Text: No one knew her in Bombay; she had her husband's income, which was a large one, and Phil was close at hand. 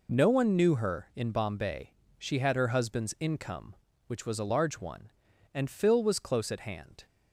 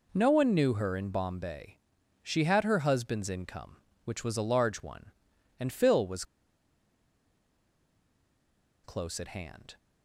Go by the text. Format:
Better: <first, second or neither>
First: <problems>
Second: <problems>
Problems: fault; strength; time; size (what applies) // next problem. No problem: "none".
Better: first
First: none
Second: pauses between "was" and "close"; strong; at 6.2 s; 2.5 s long